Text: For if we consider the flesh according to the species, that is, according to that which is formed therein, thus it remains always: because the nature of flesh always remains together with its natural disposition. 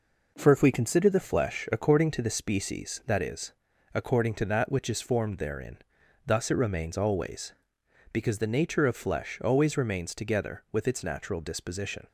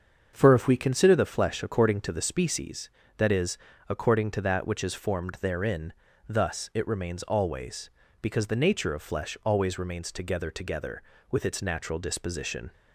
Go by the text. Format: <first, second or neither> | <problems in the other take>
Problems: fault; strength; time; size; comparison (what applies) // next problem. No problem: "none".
first | starts louder than the rest; until 1.3 s; 7 dB // says "together" twice; at 10.5 s